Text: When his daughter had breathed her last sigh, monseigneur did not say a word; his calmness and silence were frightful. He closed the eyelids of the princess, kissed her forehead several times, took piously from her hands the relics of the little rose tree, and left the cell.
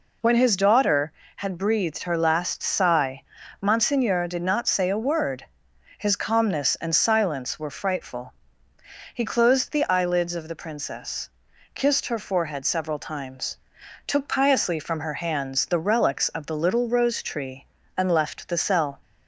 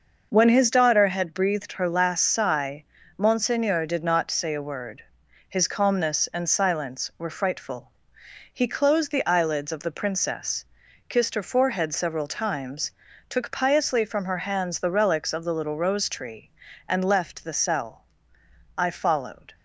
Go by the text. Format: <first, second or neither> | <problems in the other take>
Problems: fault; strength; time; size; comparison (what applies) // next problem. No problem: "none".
first | goes on to say "I followed"; noticeable; from 18.7 s on; 0.76 s long